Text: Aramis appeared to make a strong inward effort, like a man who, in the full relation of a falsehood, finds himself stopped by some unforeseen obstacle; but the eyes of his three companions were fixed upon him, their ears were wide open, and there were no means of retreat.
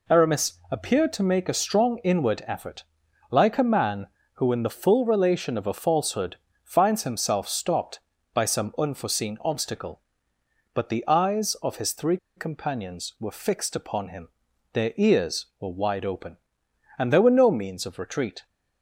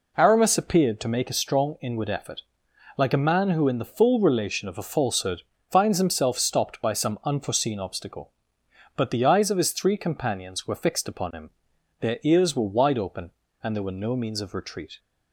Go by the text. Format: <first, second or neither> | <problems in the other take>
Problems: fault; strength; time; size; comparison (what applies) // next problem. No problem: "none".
second | pauses between "three" and "companions"; slight; at 12.1 s; 0.20 s long